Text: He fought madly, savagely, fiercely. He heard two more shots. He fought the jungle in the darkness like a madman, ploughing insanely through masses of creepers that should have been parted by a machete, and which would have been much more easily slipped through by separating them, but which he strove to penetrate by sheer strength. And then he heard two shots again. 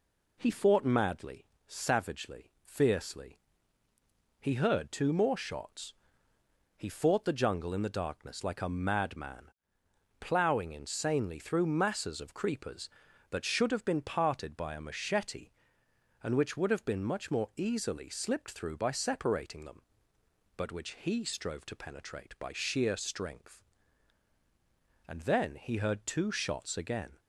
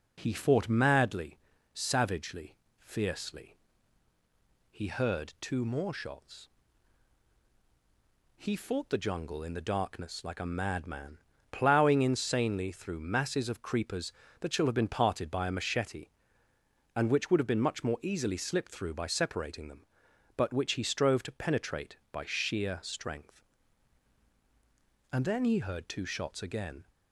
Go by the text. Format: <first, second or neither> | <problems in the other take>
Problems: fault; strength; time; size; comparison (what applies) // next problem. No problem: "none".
first | says "shall" for "should"; at 14.5 s